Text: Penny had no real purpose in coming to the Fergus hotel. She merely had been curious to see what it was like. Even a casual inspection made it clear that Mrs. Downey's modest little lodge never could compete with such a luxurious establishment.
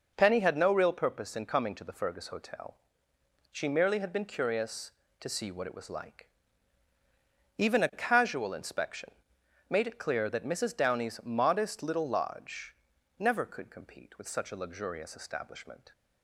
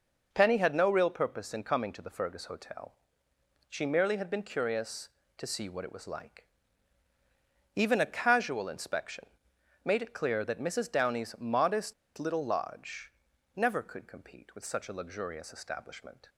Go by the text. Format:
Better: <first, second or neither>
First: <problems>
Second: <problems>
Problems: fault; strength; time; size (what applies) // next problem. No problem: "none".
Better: first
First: pauses between "inspection" and "made"; noticeable; at 9.0 s; 0.60 s long // pauses between "lodge" and "never"; noticeable; at 12.7 s; 0.46 s long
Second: pauses between "inspection" and "made"; noticeable; at 9.2 s; 0.60 s long // pauses between "modest" and "little"; slight; at 11.9 s; 0.24 s long // pauses between "lodge" and "never"; noticeable; at 13.1 s; 0.46 s long